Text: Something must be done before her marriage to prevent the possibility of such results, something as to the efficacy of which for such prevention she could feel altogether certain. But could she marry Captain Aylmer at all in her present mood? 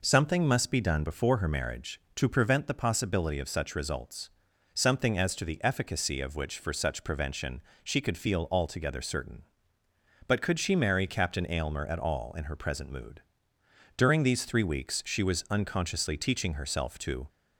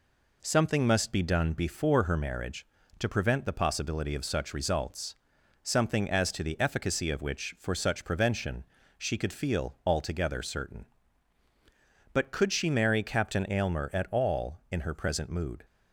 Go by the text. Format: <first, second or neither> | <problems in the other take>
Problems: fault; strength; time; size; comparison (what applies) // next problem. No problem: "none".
second | pauses between "prevention" and "she"; slight; at 7.5 s; 0.24 s long; slight in the second // goes on to say "During these three weeks she was unconsciously teaching herself to"; strong; from 13.9 s on; 3.2 s long